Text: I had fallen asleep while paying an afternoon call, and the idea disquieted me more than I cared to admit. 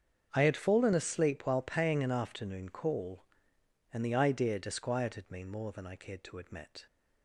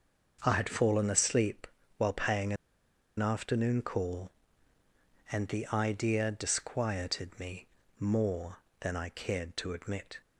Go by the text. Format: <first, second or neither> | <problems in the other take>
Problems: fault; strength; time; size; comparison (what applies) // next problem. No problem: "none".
first | starts louder than the rest; until 1.4 s; 6.5 dB; strong in the first // pauses between "asleep" and "while"; slight; at 1.6 s; 0.30 s long // pauses between "paying" and "an"; noticeable; at 2.5 s; 0.63 s long // pauses between "me" and "more"; slight; at 7.6 s; 0.32 s long